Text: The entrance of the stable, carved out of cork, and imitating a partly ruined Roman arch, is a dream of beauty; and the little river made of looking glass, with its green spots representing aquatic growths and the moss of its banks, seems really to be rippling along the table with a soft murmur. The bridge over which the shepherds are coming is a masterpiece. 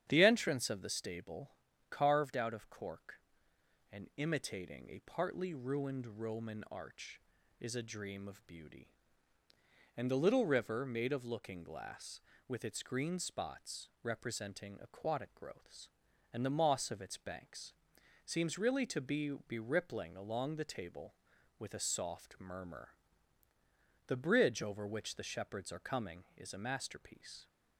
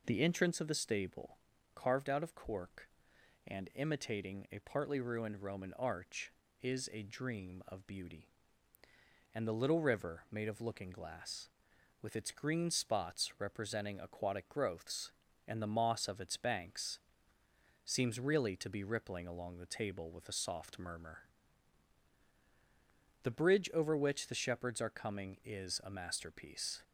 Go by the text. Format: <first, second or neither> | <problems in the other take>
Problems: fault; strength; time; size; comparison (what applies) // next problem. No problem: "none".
second | starts louder than the rest; strong; until 1.1 s; 9.5 dB // says "be" twice; at 19.4 s